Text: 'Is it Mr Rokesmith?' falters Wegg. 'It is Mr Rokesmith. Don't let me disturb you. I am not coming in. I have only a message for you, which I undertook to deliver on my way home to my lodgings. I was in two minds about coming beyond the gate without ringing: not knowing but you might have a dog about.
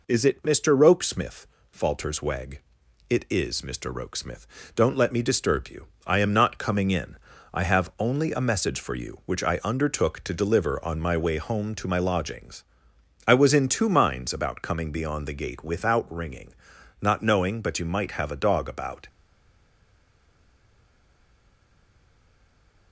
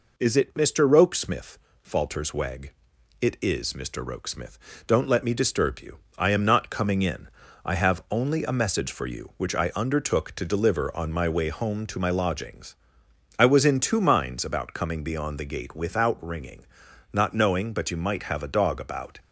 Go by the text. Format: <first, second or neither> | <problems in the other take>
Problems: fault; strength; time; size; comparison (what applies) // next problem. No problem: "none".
second | stays silent after the last word; strong; from 19.0 s on; 3.9 s long